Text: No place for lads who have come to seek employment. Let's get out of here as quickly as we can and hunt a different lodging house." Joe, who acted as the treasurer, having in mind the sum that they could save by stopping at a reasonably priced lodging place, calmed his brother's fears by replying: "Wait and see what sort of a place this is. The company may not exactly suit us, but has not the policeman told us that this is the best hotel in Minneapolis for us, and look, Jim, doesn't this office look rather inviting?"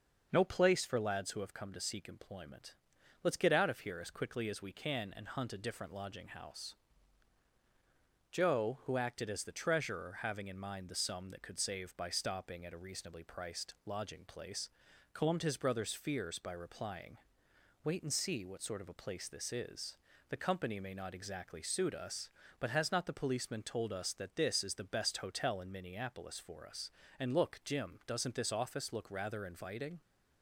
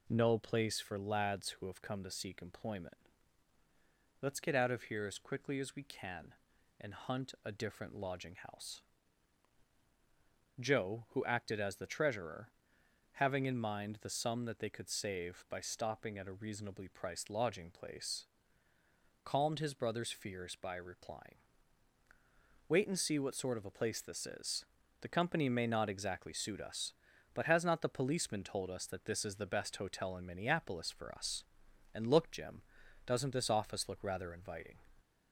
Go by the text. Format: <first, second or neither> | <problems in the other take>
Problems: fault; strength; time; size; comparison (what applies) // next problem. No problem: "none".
second | starts louder than the rest; until 1.3 s; 6.5 dB // skips "they"; at 11.4 s